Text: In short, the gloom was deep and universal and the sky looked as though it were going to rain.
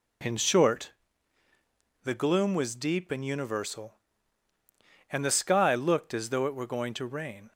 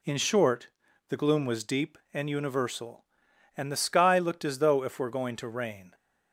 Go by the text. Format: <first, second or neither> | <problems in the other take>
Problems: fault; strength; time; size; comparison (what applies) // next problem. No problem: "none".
first | says "if" for "it"; at 4.8 s